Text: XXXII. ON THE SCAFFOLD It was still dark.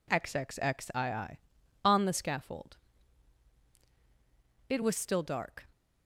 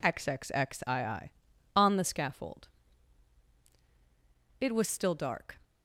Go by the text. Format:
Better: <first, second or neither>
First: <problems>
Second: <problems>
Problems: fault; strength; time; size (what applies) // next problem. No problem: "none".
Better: neither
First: pauses between "SCAFFOLD" and "It"; strong; at 2.7 s; 1.9 s long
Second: pauses between "SCAFFOLD" and "It"; strong; at 2.6 s; 1.9 s long